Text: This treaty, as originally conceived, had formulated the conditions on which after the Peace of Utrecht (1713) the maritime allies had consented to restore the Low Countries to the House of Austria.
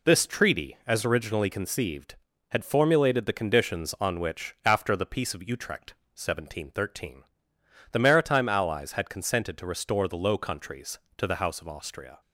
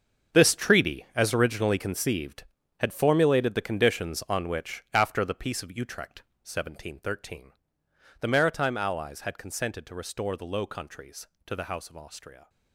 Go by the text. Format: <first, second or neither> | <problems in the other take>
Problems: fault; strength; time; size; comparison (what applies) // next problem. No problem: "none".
first | gets quieter; strong; throughout; 13.5 dB